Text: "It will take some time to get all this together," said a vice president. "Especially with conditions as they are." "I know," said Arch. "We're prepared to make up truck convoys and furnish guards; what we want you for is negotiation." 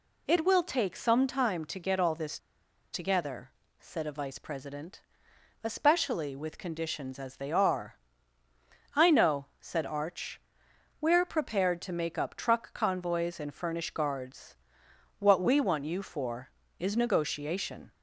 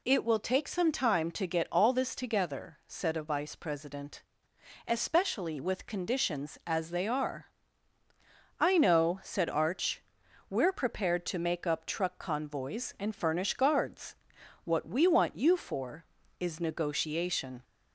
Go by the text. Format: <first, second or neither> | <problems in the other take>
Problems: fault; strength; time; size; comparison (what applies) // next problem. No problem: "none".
second | pauses between "this" and "together"; noticeable; at 2.3 s; 0.53 s long